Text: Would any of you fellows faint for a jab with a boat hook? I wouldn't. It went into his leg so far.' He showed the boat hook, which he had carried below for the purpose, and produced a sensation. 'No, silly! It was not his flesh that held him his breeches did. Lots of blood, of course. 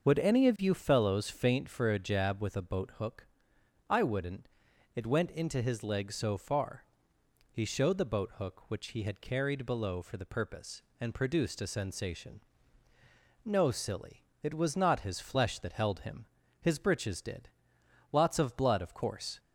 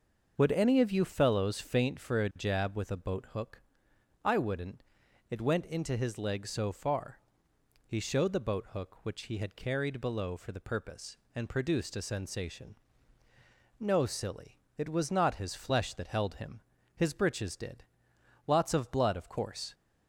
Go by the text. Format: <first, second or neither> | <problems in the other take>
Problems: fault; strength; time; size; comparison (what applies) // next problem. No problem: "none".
neither | starts louder than the rest; the same in both // pauses between "him" and "his"; slight; the same in both